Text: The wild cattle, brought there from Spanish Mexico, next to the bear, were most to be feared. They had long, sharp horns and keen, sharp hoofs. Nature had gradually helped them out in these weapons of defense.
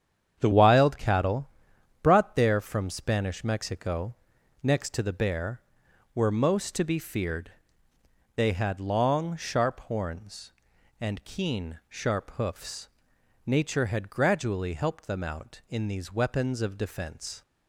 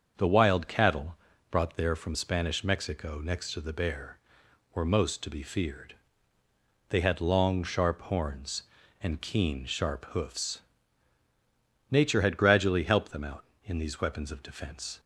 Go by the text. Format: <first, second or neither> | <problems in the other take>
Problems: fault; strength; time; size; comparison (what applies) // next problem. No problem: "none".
second | starts louder than the rest; strong; until 1.4 s; 8.5 dB; also in the second // changes voice at "wild"; from 0.5 s on; 16.9 s long